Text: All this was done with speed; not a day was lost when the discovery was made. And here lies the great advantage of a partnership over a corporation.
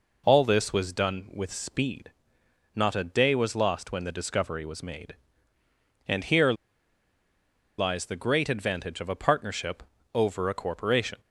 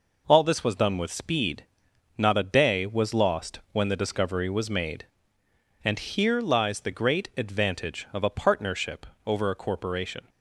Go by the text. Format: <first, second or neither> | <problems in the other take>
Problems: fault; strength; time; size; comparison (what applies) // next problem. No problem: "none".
second | pauses between "here" and "lies"; strong; at 6.5 s; 1.2 s long // pauses between "partnership" and "over"; slight; at 9.8 s; 0.28 s long; slight in the second